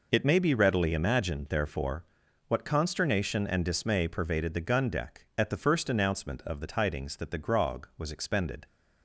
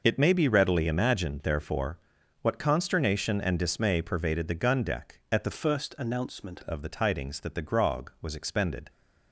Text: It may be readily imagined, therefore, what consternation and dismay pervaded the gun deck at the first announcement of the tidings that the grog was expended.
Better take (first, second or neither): first